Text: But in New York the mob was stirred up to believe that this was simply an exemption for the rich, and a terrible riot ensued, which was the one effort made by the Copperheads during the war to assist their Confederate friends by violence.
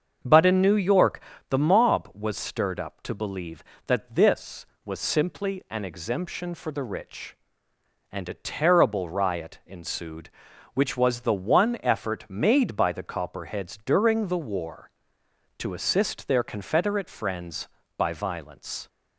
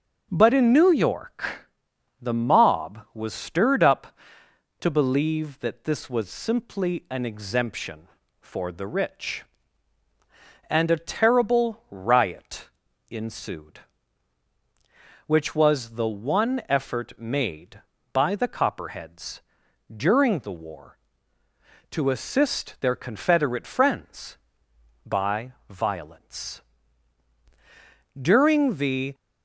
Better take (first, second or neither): first